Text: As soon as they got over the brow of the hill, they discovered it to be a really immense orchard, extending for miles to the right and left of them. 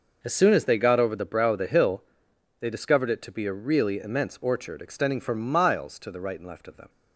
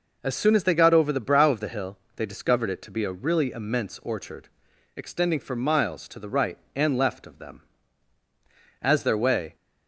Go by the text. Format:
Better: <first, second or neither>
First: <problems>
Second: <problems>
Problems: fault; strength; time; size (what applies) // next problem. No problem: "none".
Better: first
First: none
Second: goes on to say "As their way"; noticeable; from 8.8 s on; 0.74 s long